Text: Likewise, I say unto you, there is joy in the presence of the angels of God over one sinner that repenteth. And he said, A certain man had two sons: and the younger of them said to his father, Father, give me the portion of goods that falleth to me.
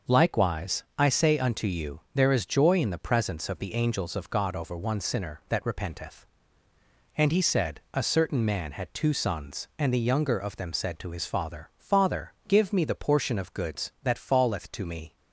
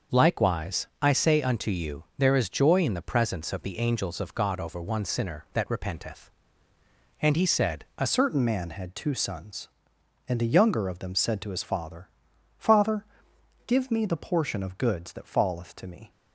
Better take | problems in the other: first | starts louder than the rest; noticeable; until 1.2 s; 6 dB // changes voice at "certain"; from 8.0 s on; 8.1 s long

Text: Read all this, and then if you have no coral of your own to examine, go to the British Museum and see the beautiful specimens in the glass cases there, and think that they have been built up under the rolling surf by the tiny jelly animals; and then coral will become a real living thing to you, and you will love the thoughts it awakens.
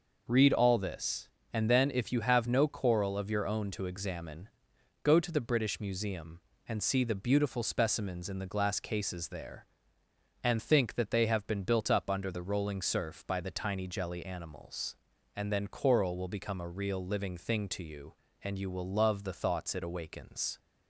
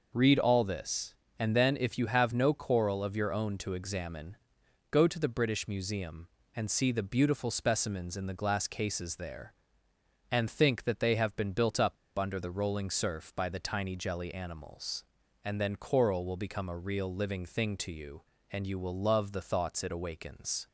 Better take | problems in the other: first | pauses between "up" and "under"; slight; at 11.9 s; 0.21 s long

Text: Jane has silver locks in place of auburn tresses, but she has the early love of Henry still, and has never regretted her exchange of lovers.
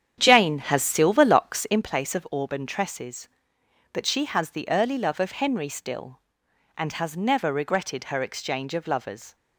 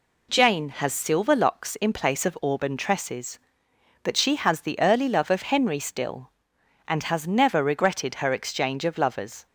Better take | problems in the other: second | starts louder than the rest; strong; until 1.8 s; 8.5 dB

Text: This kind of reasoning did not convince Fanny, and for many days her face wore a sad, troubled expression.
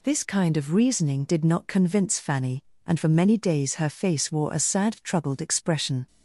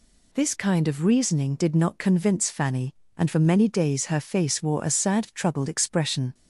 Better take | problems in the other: neither | none

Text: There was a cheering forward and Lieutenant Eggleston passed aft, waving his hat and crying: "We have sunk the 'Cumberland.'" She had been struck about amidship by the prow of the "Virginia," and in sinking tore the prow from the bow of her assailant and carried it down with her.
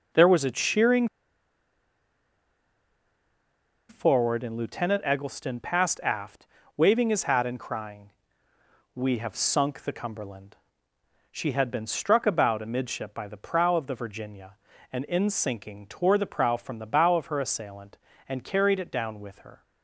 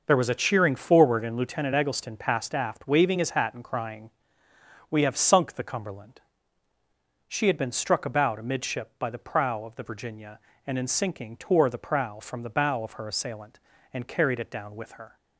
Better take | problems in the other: second | pauses between "cheering" and "forward"; strong; at 1.0 s; 2.8 s long

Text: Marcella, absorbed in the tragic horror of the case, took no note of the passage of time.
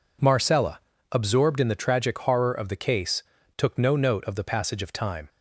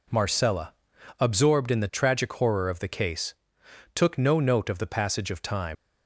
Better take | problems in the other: first | leaves "time" unfinished; at 5.7 s; 60 ms

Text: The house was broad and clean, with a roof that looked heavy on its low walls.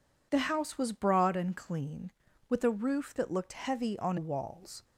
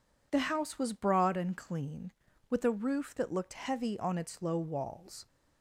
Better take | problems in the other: second | skips "its low"; at 4.1 s

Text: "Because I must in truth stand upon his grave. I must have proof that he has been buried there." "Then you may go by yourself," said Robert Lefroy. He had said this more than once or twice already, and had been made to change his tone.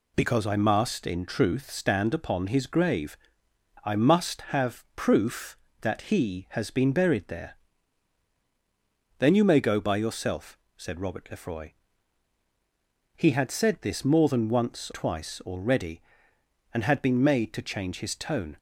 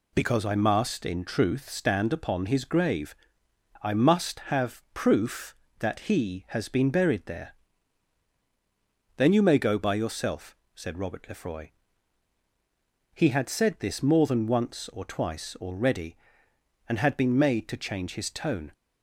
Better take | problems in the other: second | skips "or"; at 14.9 s

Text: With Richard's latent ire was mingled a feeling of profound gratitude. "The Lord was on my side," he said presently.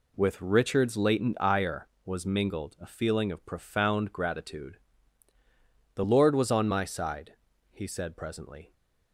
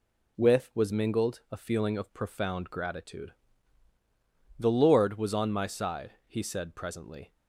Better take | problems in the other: first | skips "Richard's latent ire"; at 0.7 s

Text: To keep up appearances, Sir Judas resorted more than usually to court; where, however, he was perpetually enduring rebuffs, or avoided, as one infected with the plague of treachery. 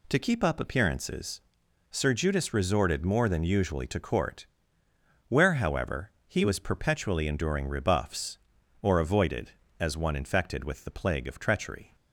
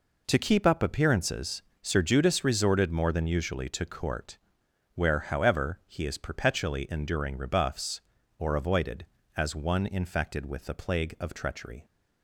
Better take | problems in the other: first | says "is" for "was"; at 6.0 s

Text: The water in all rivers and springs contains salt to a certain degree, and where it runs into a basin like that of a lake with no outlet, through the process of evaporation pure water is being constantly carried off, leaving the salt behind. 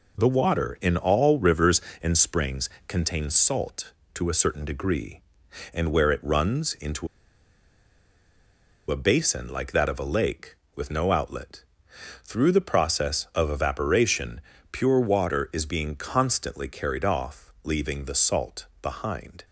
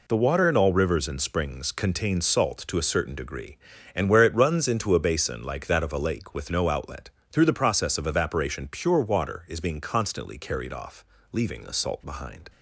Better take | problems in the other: second | pauses between "springs" and "contains"; slight; at 2.6 s; 0.18 s long // pauses between "into" and "a"; strong; at 7.0 s; 1.8 s long // pauses between "evaporation" and "pure"; slight; at 14.4 s; 0.30 s long // pauses between "salt" and "behind"; slight; at 18.6 s; 0.16 s long

